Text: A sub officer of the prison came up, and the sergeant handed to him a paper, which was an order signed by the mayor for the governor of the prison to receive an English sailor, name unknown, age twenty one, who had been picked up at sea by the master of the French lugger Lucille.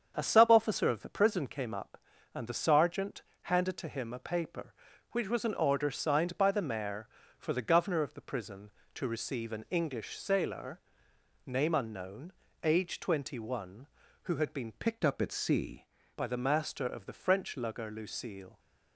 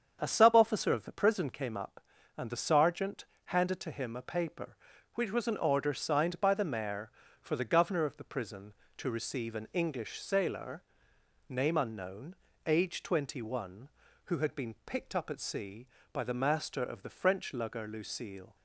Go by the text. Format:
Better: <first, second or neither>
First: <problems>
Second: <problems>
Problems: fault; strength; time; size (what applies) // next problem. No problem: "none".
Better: second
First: starts louder than the rest; strong; until 1.1 s; 7.5 dB // pauses between "sergeant" and "handed"; slight; at 3.2 s; 0.22 s long // changes voice from "picked" to "sea"; from 14.7 to 15.8 s; 1.1 s long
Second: starts louder than the rest; strong; until 1.2 s; 7.5 dB // pauses between "sergeant" and "handed"; slight; at 3.2 s; 0.22 s long